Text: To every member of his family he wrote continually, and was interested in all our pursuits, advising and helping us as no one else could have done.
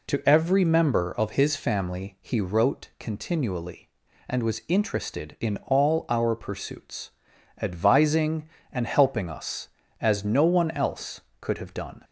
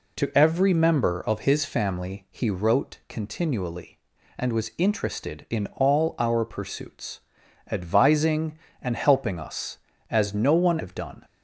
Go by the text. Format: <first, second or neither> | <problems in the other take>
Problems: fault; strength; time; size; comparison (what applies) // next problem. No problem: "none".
first | skips "else could"; at 10.7 s